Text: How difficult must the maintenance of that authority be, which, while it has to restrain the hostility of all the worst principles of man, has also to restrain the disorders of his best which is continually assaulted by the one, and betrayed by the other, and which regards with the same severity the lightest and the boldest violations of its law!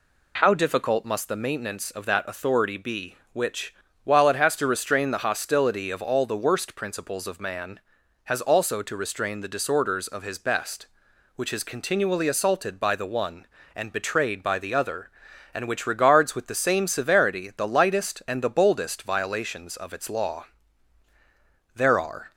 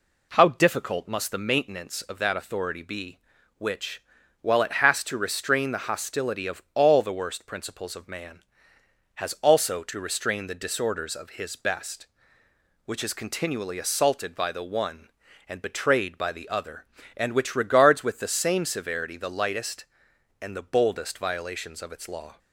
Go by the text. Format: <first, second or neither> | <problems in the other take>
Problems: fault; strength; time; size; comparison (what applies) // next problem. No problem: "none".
second | goes on to say "There are"; from 21.7 s on; 0.56 s long